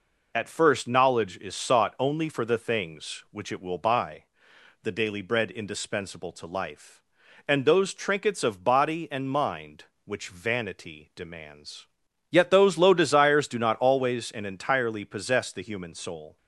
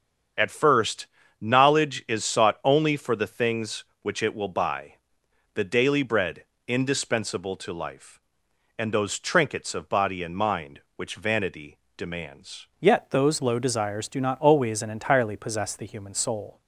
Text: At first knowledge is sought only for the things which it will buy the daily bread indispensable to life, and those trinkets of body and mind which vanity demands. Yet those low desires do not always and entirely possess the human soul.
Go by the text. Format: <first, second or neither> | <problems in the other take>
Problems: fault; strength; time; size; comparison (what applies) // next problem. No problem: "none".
first | starts louder than the rest; strong; until 1.7 s; 7.5 dB // pauses between "first" and "knowledge"; slight; at 1.0 s; 0.34 s long // pauses between "buy" and "the"; noticeable; at 4.9 s; 0.62 s long; noticeable in the first // pauses between "bread" and "indispensable"; slight; at 6.4 s; 0.24 s long // pauses between "vanity" and "demands"; slight; at 11.7 s; 0.18 s long // changes voice at "Yet"; from 12.7 s on; 3.9 s long